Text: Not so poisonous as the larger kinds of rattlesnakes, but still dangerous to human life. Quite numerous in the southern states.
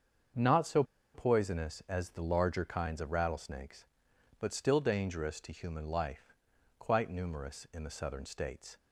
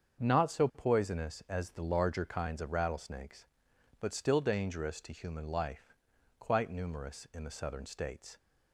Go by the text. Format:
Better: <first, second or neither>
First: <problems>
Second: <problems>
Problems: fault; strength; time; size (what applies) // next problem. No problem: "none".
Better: second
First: starts louder than the rest; until 1.6 s; 7 dB // pauses between "so" and "poisonous"; slight; at 0.8 s; 0.31 s long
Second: starts louder than the rest; until 1.2 s; 7 dB